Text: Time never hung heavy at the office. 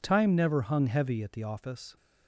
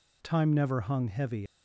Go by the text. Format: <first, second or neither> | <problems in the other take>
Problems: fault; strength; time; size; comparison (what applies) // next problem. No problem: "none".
first | stops before "at the office"; at 1.4 s